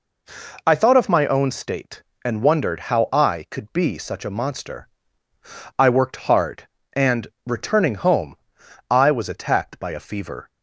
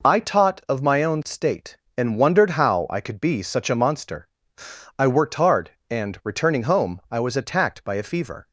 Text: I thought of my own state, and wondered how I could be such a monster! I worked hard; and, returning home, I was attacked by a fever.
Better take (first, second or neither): first